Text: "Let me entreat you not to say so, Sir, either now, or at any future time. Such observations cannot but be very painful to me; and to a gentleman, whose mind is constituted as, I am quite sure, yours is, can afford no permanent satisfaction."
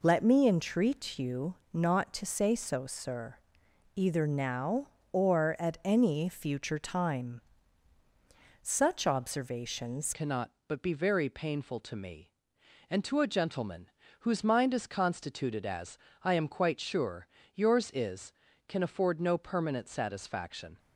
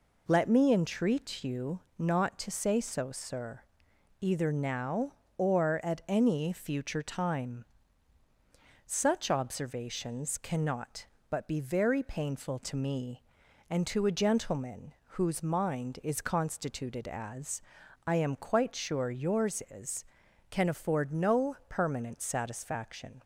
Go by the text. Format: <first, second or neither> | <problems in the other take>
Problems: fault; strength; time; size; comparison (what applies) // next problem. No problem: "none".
second | pauses between "you" and "not"; slight; at 1.5 s; 0.18 s long; slight in the second // changes voice at "cannot"; from 10.1 s on; 10.6 s long